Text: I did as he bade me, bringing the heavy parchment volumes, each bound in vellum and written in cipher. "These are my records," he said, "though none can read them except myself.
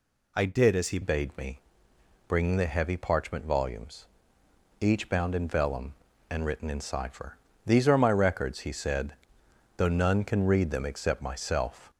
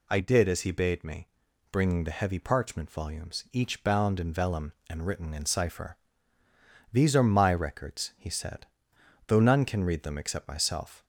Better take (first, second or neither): second